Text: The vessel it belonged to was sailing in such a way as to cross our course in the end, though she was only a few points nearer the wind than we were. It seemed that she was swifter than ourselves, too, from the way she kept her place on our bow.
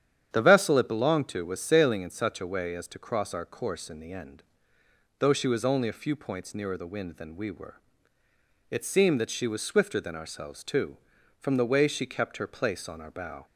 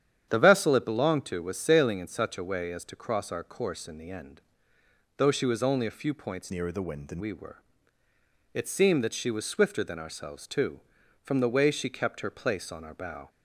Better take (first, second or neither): first